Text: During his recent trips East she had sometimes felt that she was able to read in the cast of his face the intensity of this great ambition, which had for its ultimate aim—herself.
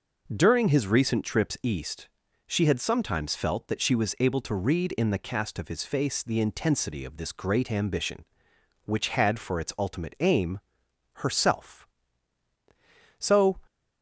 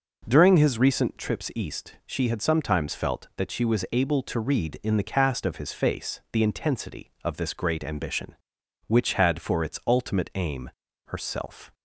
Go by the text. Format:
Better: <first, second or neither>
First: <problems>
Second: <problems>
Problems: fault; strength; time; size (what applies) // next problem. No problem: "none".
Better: second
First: pauses between "East" and "she"; at 2.0 s; 0.40 s long // goes on to say "So"; slight; from 13.1 s on; 0.42 s long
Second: none